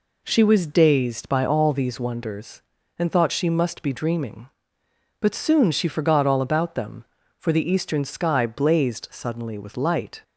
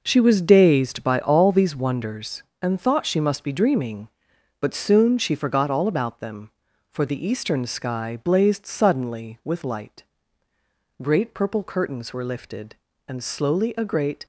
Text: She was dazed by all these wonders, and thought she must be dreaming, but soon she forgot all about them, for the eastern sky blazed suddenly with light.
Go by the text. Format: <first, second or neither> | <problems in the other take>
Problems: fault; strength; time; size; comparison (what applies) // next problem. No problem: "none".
first | goes on to say "Great purple curtains were lifted and slowly a great"; strong; from 11.0 s on; 3.2 s long